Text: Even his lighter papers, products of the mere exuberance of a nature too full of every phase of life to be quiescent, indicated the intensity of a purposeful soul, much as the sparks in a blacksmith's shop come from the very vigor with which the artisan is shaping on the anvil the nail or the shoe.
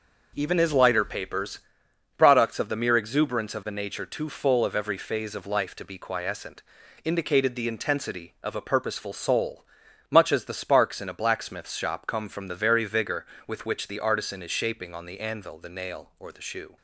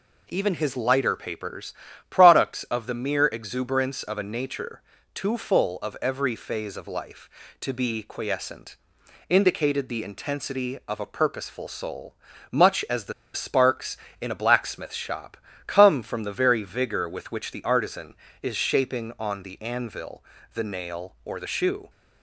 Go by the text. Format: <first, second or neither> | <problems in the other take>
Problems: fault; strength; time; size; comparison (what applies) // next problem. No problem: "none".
first | pauses between "nature" and "too"; slight; at 4.8 s; 0.32 s long // pauses between "the" and "sparks"; slight; at 13.1 s; 0.22 s long // pauses between "shop" and "come"; slight; at 15.3 s; 0.30 s long // pauses between "anvil" and "the"; slight; at 20.2 s; 0.30 s long